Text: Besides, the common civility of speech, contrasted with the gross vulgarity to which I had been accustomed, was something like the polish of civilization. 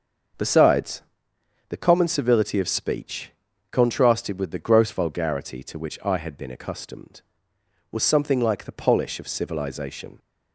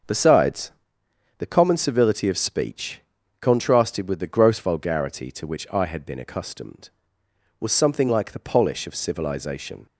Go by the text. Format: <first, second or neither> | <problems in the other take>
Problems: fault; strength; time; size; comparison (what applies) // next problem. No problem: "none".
neither | starts louder than the rest; the same in both